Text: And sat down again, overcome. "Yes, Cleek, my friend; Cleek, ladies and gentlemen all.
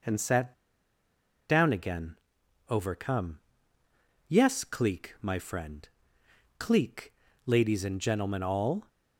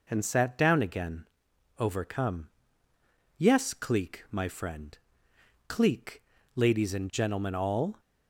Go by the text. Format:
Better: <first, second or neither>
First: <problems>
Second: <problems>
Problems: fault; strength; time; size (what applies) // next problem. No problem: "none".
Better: second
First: pauses between "sat" and "down"; noticeable; at 0.5 s; 0.96 s long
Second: none